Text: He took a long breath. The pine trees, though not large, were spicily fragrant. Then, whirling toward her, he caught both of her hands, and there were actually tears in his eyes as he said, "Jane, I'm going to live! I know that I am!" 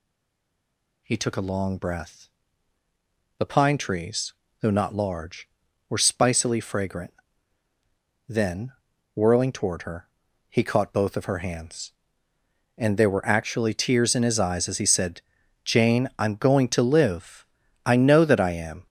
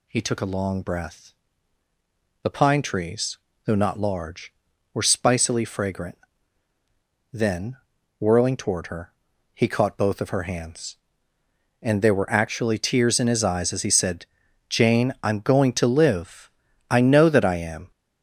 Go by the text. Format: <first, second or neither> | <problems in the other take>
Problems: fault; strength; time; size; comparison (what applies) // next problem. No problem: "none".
second | stays silent before the first word; until 1.0 s; 1.0 s long